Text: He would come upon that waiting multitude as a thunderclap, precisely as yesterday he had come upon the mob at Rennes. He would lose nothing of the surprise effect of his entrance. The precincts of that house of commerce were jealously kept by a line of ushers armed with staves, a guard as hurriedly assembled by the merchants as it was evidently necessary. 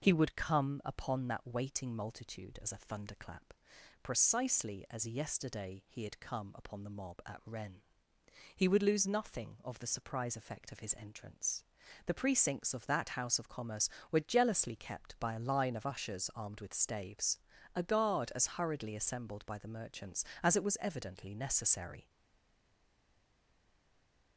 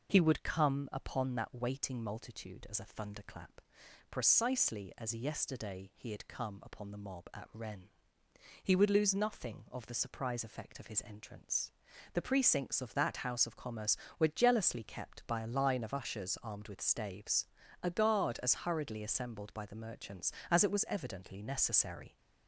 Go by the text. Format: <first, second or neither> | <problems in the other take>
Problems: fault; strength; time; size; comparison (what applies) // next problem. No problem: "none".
second | stays silent after the last word; from 22.0 s on; 2.3 s long